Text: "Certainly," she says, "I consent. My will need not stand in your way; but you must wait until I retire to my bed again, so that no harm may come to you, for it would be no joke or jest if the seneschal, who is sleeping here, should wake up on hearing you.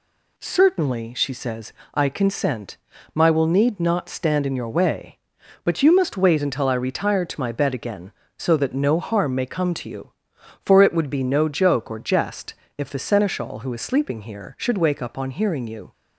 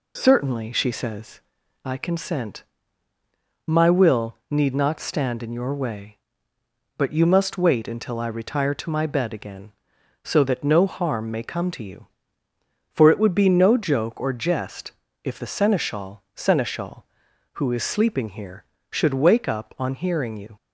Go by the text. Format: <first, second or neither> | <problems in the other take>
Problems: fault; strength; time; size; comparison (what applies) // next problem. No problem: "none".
first | pauses between "jest" and "if"; slight; at 14.9 s; 0.30 s long; slight in the first // says "seneschal" twice; at 16.3 s